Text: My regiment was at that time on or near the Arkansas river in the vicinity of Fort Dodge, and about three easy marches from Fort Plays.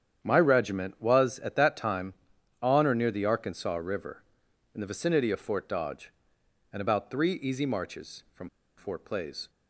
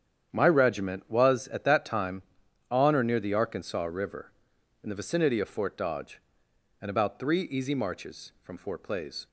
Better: second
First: starts louder than the rest; strong; until 1.2 s; 9 dB // pauses between "from" and "Fort"; slight; at 8.4 s; 0.28 s long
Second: starts louder than the rest; strong; until 1.3 s; 9 dB

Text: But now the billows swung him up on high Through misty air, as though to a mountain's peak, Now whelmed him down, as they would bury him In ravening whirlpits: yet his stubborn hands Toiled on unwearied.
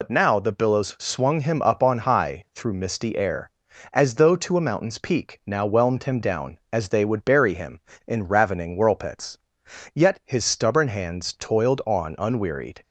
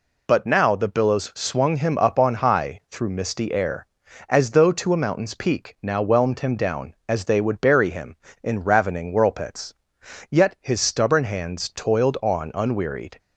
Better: second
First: loses the start of "But"; at 0.0 s; 85 ms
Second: none

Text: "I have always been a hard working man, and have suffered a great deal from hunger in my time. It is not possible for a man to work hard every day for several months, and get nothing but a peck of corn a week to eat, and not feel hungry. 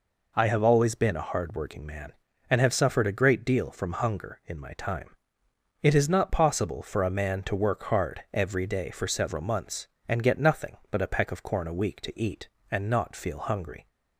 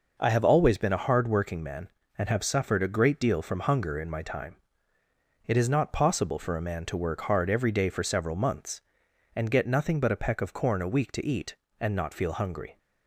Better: neither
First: none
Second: none

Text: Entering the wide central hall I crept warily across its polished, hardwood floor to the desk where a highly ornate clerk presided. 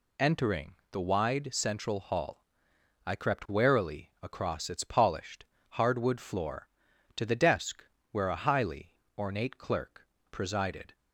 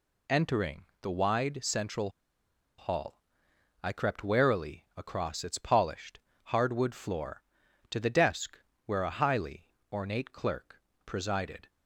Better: first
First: pauses between "Entering" and "the"; slight; at 0.7 s; 0.18 s long // pauses between "hall" and "I"; noticeable; at 2.4 s; 0.64 s long // pauses between "desk" and "where"; slight; at 7.8 s; 0.28 s long // pauses between "highly" and "ornate"; slight; at 8.9 s; 0.20 s long // pauses between "clerk" and "presided"; slight; at 10.0 s; 0.24 s long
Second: pauses between "Entering" and "the"; slight; at 0.8 s; 0.18 s long // pauses between "central" and "hall"; noticeable; at 2.0 s; 0.69 s long // pauses between "hall" and "I"; noticeable; at 3.1 s; 0.64 s long // pauses between "desk" and "where"; slight; at 8.5 s; 0.28 s long // pauses between "highly" and "ornate"; slight; at 9.6 s; 0.20 s long // pauses between "clerk" and "presided"; slight; at 10.8 s; 0.24 s long

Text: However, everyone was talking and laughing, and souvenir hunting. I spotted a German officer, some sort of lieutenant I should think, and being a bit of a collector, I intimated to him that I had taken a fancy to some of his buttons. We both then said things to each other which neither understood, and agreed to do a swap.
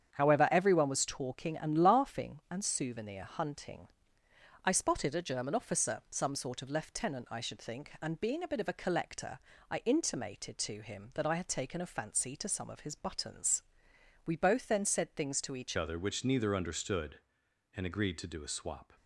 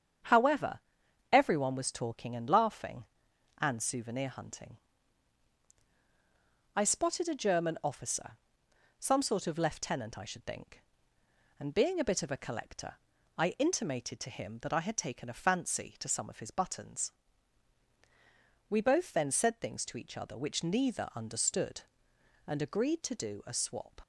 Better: second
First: starts louder than the rest; strong; until 1.1 s; 8.5 dB // changes voice at "other"; from 15.7 s on; 3.2 s long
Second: starts louder than the rest; strong; until 1.7 s; 8 dB

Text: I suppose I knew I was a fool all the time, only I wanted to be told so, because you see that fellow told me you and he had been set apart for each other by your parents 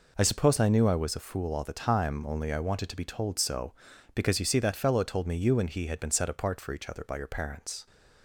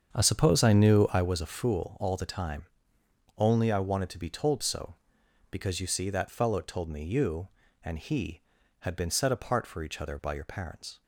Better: first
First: none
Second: starts louder than the rest; strong; until 1.3 s; 7.5 dB

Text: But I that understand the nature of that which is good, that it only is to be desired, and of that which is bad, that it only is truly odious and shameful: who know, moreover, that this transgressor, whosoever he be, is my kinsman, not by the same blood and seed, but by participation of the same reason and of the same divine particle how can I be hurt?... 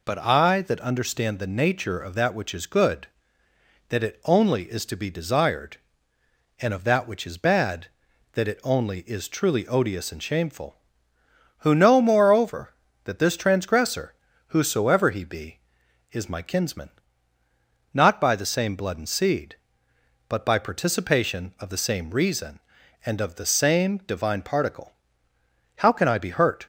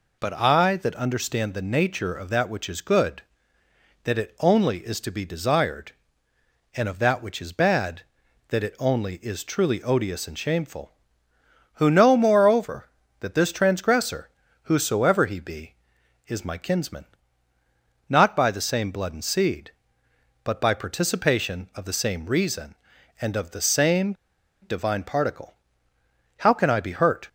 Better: first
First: pauses between "particle" and "how"; noticeable; at 24.9 s; 0.84 s long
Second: pauses between "same" and "divine"; noticeable; at 24.1 s; 0.47 s long // pauses between "particle" and "how"; noticeable; at 25.5 s; 0.84 s long

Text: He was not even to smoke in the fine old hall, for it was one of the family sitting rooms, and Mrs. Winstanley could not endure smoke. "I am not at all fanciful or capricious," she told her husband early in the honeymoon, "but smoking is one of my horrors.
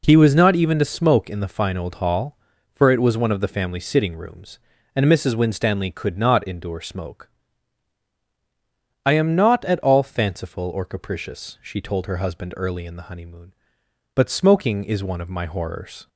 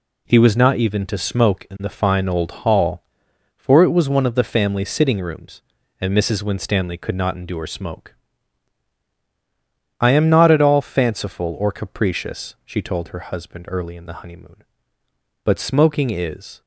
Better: first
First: none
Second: stops before "one of my horrors"; at 16.6 s

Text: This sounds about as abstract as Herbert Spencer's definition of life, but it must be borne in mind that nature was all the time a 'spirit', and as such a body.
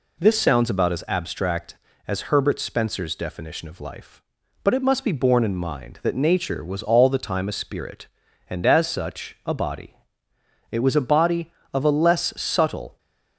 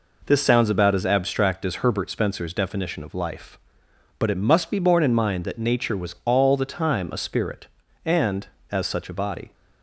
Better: second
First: goes on to say "It was a body of a less subtle"; strong; from 10.7 s on; 2.2 s long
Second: none

